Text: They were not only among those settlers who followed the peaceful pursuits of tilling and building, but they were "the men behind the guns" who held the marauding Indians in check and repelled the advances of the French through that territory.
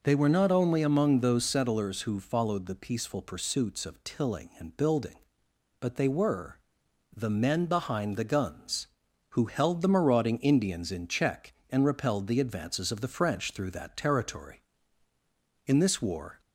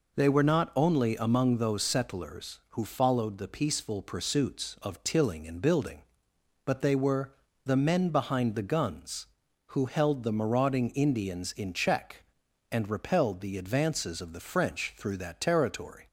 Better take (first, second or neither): second